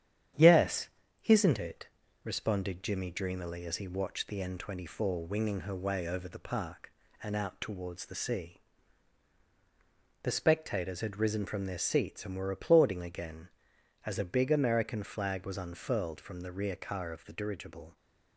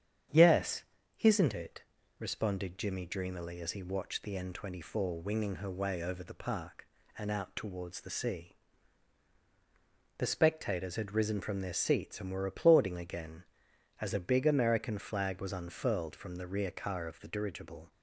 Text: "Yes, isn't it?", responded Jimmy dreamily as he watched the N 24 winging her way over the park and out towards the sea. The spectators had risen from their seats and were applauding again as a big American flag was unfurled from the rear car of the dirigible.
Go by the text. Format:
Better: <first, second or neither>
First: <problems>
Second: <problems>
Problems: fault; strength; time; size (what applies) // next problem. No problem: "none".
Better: second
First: gets quieter; slight; throughout; 3 dB // starts louder than the rest; strong; until 1.7 s; 9.5 dB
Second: starts louder than the rest; strong; until 1.6 s; 8.5 dB